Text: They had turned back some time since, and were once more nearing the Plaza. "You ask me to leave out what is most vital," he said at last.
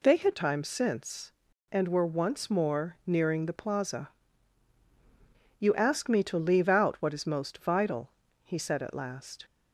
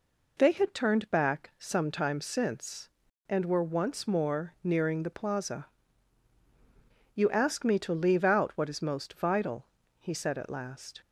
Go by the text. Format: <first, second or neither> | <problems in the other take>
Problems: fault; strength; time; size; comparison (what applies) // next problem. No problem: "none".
second | skips "turned back some"; at 0.3 s